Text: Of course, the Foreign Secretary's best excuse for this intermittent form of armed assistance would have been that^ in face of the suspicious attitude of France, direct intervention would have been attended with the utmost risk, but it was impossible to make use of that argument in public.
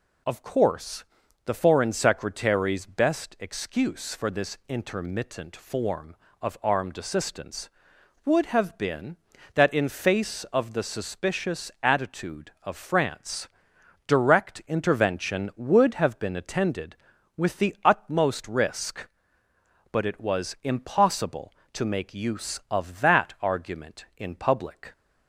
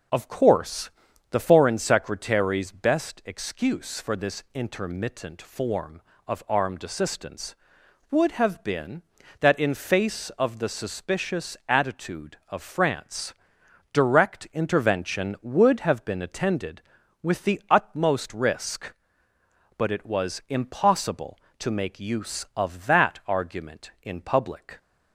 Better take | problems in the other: first | starts louder than the rest; noticeable; until 1.7 s; 6 dB

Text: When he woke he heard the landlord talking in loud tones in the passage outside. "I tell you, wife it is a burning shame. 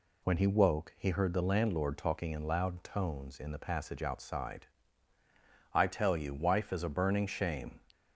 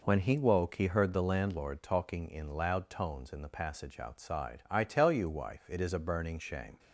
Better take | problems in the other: second | skips "it"; at 6.7 s

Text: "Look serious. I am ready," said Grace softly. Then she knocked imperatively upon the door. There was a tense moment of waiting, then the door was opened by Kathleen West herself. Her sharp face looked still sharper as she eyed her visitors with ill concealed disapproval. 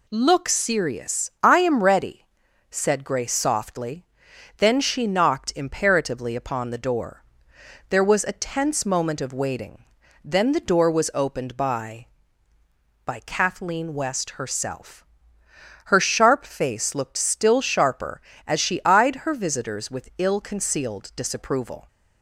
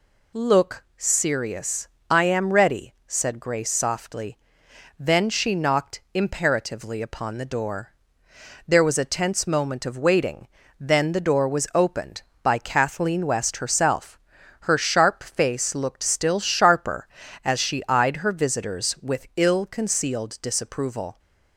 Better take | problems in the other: second | says "by" twice; at 13.0 s

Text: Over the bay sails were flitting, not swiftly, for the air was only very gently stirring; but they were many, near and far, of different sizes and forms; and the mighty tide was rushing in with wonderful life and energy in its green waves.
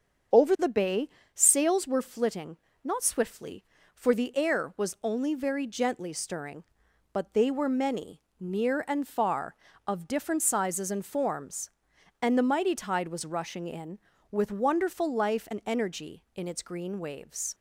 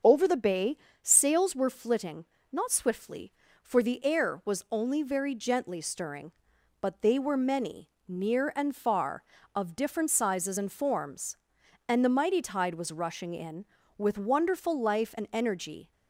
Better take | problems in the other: first | starts louder than the rest; until 1.2 s; 7 dB; also in the first // pauses between "bay" and "sails"; slight; at 0.7 s; 0.24 s long; slight in the first // stops before "in its green waves"; at 15.9 s

